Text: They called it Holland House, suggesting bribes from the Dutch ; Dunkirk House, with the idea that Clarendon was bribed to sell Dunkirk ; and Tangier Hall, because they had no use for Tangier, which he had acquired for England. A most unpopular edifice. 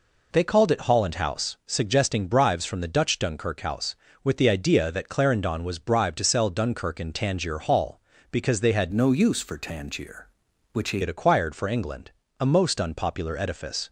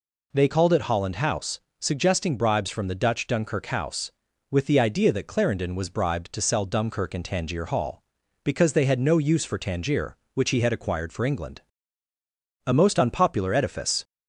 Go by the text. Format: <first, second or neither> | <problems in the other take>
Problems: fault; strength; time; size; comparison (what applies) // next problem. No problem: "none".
second | changes voice from "no" to "he"; from 8.9 to 10.9 s; 2.0 s long